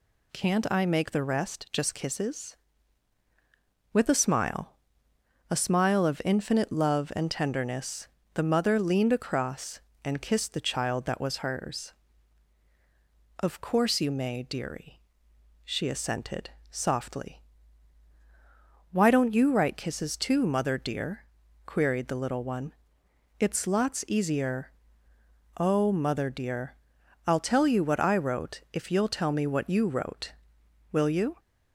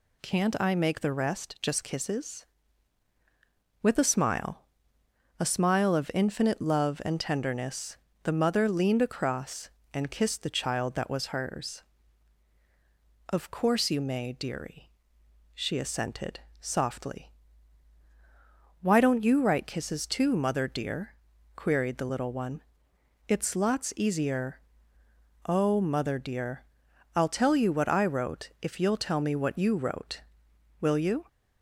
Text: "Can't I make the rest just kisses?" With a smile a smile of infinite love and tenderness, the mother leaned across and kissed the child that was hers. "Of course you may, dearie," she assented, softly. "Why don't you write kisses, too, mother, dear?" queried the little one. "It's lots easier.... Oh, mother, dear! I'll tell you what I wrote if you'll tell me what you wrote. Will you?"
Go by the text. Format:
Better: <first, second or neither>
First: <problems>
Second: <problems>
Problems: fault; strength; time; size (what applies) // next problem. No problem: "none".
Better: neither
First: pauses between "smile" and "a"; noticeable; at 4.7 s; 0.74 s long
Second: pauses between "smile" and "a"; noticeable; at 4.6 s; 0.74 s long